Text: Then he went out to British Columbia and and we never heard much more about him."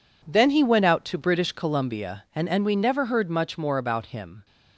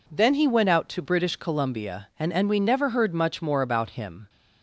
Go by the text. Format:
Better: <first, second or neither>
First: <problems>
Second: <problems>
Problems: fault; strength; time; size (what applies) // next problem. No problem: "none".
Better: second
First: gets quieter; strong; throughout; 12 dB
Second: none